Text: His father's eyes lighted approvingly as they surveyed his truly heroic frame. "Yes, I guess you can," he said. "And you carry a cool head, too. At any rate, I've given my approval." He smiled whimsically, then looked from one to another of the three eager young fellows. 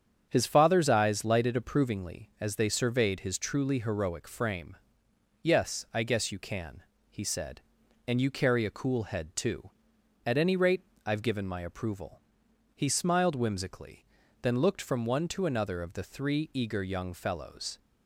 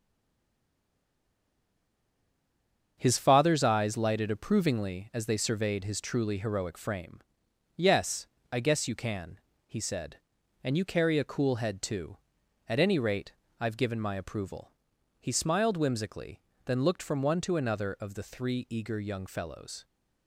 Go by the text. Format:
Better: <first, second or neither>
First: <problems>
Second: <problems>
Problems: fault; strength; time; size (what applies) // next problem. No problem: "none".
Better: first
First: starts louder than the rest; strong; until 1.3 s; 8 dB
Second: stays silent before the first word; strong; until 2.9 s; 2.9 s long // starts louder than the rest; until 3.9 s; 7 dB